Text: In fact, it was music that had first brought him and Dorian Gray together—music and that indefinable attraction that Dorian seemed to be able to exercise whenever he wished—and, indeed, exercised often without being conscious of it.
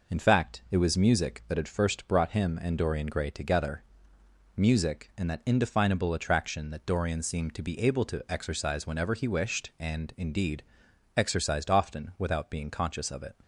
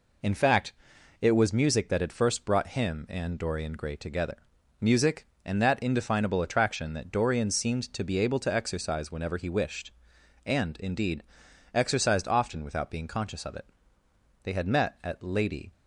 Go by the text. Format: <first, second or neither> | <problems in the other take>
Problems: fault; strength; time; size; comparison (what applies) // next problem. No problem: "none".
first | goes on to say "They had met at Lady"; noticeable; from 14.4 s on; 1.2 s long